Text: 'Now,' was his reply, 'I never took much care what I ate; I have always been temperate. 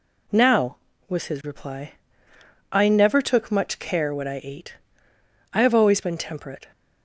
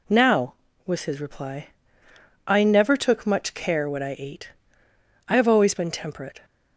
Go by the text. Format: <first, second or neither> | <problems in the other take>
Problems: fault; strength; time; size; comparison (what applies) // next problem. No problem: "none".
neither | none